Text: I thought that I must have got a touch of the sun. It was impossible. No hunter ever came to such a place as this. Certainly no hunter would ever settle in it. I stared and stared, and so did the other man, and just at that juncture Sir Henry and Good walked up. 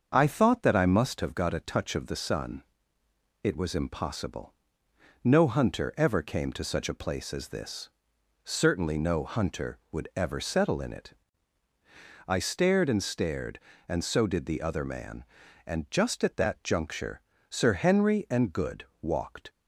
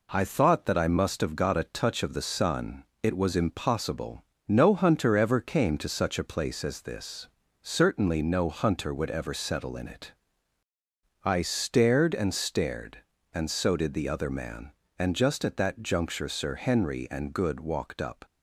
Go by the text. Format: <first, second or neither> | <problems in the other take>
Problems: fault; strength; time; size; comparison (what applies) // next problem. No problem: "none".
second | starts louder than the rest; until 1.1 s; 6.5 dB // pauses between "juncture" and "Sir"; slight; at 17.1 s; 0.30 s long // pauses between "Good" and "walked"; slight; at 18.8 s; 0.18 s long // stops before "up"; at 19.4 s